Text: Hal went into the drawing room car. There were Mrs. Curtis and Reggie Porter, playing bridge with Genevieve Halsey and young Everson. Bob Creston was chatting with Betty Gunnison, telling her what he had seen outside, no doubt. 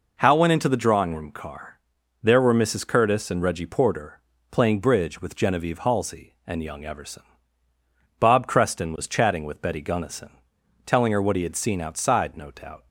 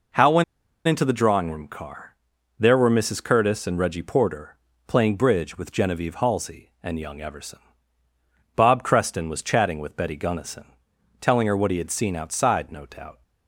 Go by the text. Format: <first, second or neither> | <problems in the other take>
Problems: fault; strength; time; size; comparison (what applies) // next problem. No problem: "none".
first | pauses between "went" and "into"; at 0.4 s; 0.44 s long